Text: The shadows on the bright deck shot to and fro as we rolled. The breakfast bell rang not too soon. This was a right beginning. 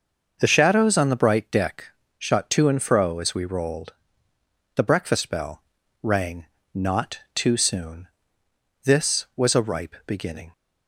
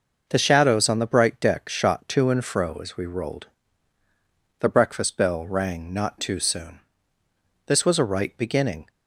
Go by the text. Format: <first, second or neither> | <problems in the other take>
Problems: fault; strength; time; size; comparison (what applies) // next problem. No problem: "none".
second | starts louder than the rest; noticeable; until 1.4 s; 6 dB // pauses between "deck" and "shot"; slight; at 1.8 s; 0.30 s long // pauses between "bell" and "rang"; at 5.6 s; 0.38 s long // pauses between "rang" and "not"; slight; at 6.4 s; 0.26 s long // pauses between "not" and "too"; slight; at 7.1 s; 0.16 s long // says "ripe" for "right"; at 9.6 s